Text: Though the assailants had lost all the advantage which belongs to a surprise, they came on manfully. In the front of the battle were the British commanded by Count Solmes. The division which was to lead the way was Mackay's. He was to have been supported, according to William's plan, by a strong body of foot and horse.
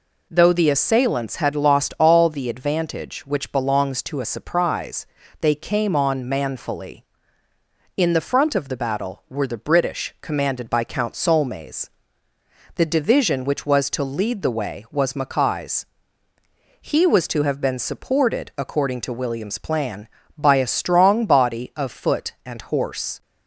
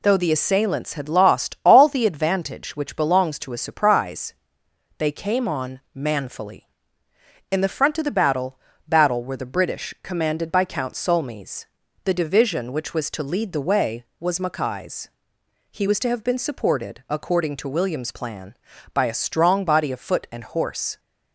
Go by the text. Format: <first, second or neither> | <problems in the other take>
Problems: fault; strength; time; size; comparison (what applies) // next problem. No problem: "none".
first | pauses between "on" and "manfully"; slight; at 5.7 s; 0.16 s long // says "battle" twice; at 8.8 s